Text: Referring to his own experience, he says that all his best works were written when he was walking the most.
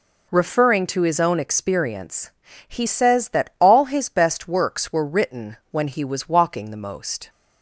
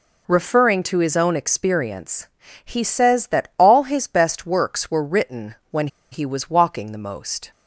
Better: first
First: none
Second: pauses between "when" and "he"; slight; at 5.8 s; 0.24 s long

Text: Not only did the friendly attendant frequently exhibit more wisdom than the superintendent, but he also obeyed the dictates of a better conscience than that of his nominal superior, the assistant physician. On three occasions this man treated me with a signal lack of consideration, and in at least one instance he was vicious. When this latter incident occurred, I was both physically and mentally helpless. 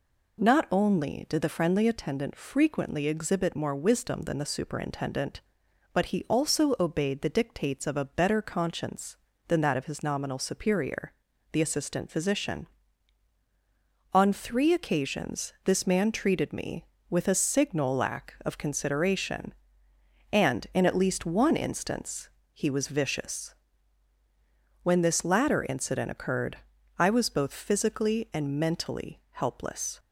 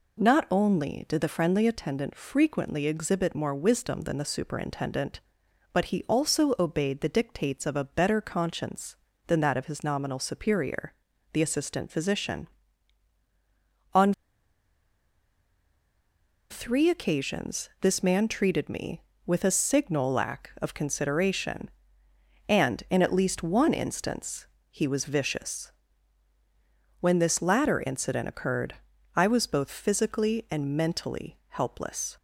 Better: first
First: pauses between "instance" and "he"; slight; at 22.2 s; 0.24 s long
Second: pauses between "On" and "three"; strong; at 14.1 s; 2.3 s long // pauses between "instance" and "he"; slight; at 24.4 s; 0.24 s long

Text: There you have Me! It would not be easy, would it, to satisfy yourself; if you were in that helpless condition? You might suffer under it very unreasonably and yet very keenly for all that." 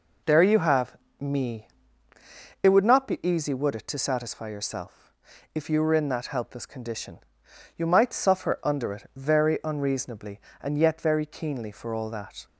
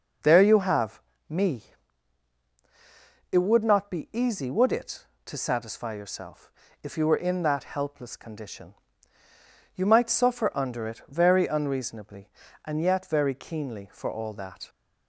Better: neither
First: pauses between "have" and "Me"; slight; at 0.9 s; 0.24 s long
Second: pauses between "have" and "Me"; slight; at 1.0 s; 0.28 s long

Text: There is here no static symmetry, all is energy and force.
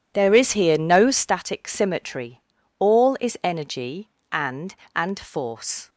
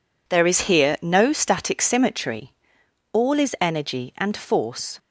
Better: second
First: says "and" twice; at 4.9 s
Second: none

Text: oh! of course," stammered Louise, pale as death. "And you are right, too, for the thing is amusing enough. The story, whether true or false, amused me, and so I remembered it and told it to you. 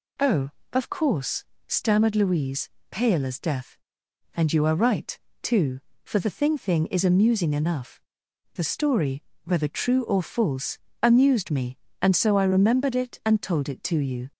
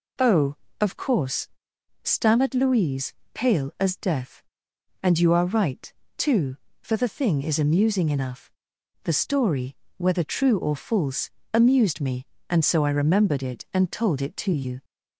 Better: second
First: says "thing" twice; at 6.5 s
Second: none

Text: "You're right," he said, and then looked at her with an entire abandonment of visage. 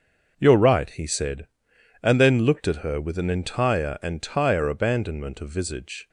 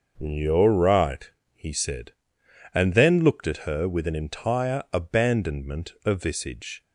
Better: second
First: starts louder than the rest; until 1.3 s; 6 dB // says "entire" twice; at 4.0 s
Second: starts louder than the rest; noticeable; until 1.1 s; 6 dB

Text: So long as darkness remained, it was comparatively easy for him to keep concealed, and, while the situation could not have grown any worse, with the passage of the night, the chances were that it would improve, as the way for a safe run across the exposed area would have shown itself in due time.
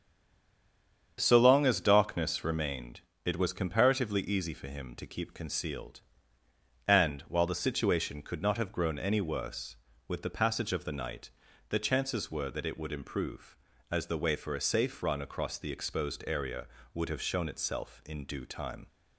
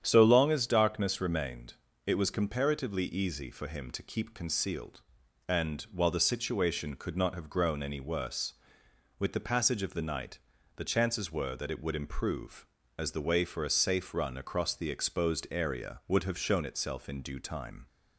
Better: second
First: stays silent before the first word; until 1.1 s; 1.1 s long // starts louder than the rest; strong; until 2.1 s; 8 dB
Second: starts louder than the rest; strong; until 1.0 s; 9 dB

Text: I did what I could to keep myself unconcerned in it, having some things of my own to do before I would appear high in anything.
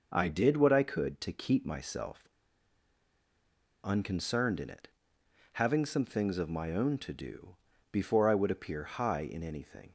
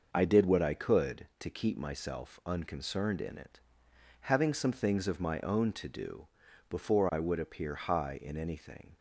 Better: second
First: pauses between "myself" and "unconcerned"; strong; at 2.2 s; 1.5 s long // pauses between "do" and "before"; at 7.5 s; 0.38 s long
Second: pauses between "do" and "before"; at 6.2 s; 0.44 s long

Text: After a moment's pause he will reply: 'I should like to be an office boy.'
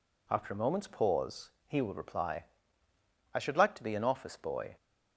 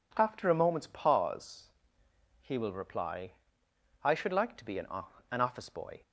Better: first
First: pauses between "pause" and "he"; slight; at 1.5 s; 0.18 s long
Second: pauses between "pause" and "he"; noticeable; at 1.7 s; 0.72 s long // says "an" twice; at 5.3 s

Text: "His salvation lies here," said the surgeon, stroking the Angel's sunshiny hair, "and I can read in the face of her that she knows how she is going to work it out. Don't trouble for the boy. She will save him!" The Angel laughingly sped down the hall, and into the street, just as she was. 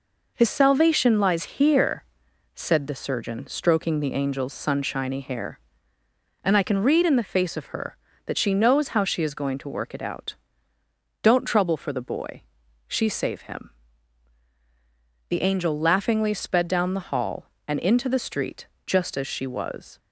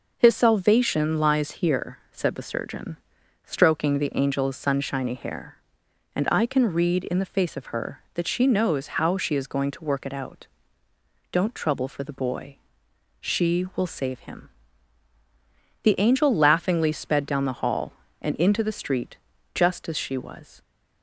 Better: second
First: skips "will"; at 13.0 s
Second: none

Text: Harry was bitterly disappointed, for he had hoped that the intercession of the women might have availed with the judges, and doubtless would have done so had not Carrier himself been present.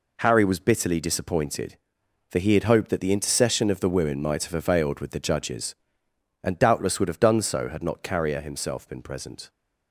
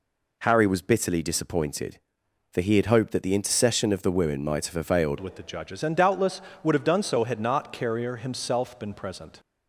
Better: first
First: none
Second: changes voice at "with"; from 5.1 s on; 4.2 s long

